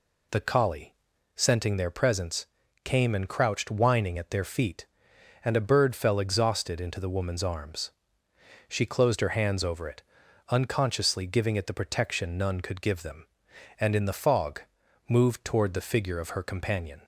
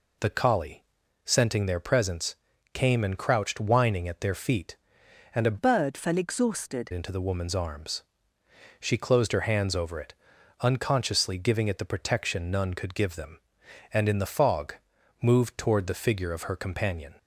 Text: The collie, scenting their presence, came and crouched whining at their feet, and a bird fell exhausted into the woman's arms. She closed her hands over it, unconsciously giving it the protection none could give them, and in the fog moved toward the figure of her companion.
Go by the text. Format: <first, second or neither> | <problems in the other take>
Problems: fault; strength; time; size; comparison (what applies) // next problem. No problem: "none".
first | changes voice from "bird" to "exhausted"; from 5.5 to 6.9 s; 1.4 s long // pauses between "fog" and "moved"; noticeable; at 14.7 s; 0.48 s long; noticeable in the first